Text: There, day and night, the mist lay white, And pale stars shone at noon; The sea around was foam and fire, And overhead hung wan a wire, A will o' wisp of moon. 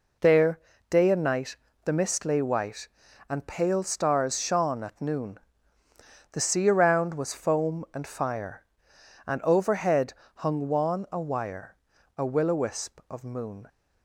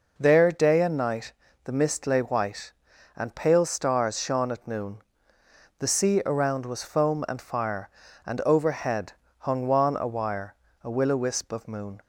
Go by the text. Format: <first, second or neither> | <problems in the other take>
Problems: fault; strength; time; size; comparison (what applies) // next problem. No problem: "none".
neither | pauses between "overhead" and "hung"; slight; the same in both